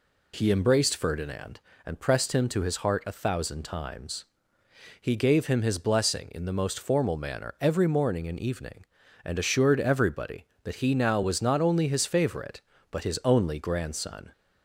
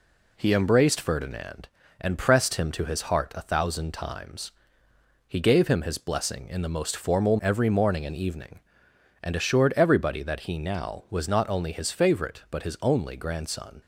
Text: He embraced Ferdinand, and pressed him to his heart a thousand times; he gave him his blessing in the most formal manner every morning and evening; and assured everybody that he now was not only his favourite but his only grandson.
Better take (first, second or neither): first